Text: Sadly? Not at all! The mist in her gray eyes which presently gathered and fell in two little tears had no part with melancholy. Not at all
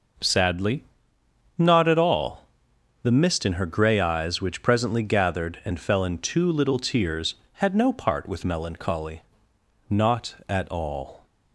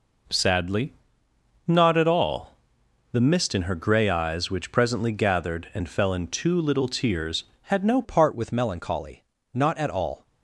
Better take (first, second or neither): first